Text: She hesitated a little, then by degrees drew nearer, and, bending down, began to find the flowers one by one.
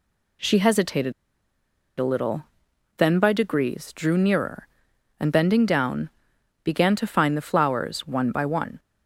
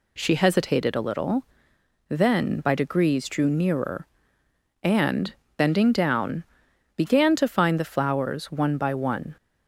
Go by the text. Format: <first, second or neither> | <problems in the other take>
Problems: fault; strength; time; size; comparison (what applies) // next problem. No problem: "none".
second | pauses between "hesitated" and "a"; noticeable; at 1.1 s; 0.86 s long